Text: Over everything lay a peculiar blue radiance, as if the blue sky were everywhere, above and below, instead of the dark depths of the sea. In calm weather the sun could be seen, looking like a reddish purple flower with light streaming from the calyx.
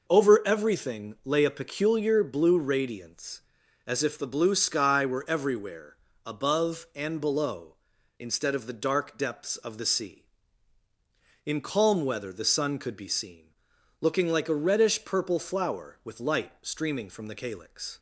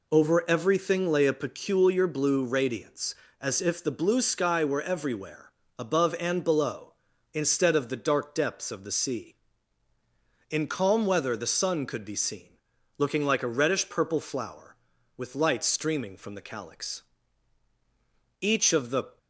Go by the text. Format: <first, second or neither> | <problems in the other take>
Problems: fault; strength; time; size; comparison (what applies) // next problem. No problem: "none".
first | goes on to say "Each of the"; noticeable; from 18.3 s on; 0.78 s long